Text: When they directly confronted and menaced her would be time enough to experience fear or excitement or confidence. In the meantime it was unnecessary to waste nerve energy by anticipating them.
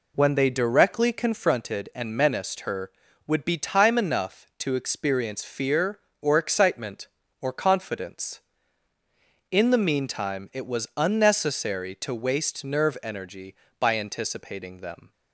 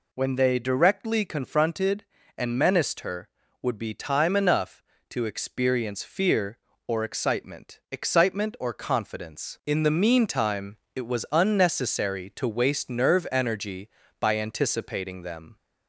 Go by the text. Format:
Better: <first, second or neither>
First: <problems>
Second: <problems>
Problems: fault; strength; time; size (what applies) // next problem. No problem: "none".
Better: first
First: none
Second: says "excitement" twice; at 7.8 s // pauses between "meantime" and "it"; slight; at 10.7 s; 0.18 s long